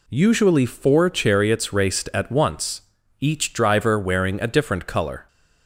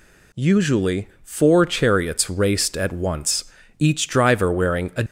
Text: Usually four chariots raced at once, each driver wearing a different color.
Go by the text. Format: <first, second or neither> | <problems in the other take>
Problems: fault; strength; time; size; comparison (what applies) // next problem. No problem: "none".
first | pauses between "Usually" and "four"; slight; at 1.0 s; 0.16 s long // stops before "different color"; at 5.0 s